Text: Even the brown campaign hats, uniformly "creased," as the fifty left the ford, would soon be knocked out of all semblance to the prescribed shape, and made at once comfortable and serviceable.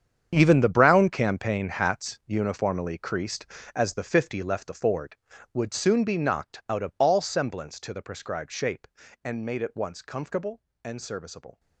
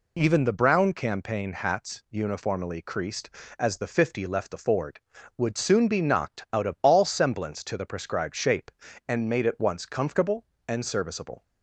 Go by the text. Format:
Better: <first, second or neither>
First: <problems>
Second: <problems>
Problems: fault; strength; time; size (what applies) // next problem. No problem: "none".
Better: second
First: gets quieter; strong; throughout; 14 dB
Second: none